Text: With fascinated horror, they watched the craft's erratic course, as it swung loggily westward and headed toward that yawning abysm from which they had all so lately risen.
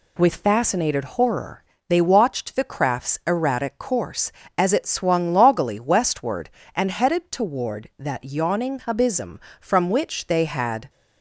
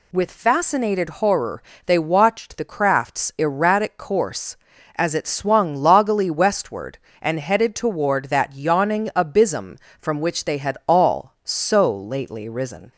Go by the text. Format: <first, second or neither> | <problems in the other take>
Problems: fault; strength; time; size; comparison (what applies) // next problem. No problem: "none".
second | stops before "all so lately risen"; at 10.8 s